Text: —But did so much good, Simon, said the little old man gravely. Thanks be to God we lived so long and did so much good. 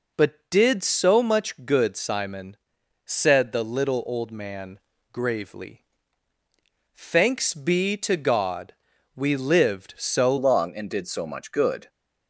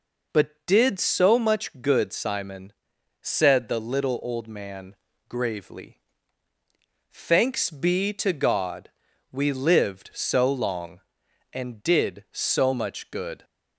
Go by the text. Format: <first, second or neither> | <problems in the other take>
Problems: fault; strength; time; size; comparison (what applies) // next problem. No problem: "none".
second | pauses between "man" and "gravely"; slight; at 4.7 s; 0.32 s long; slight in the second // pauses between "God" and "we"; at 8.7 s; 0.42 s long; also in the second // changes voice at "long"; from 10.3 s on; 1.5 s long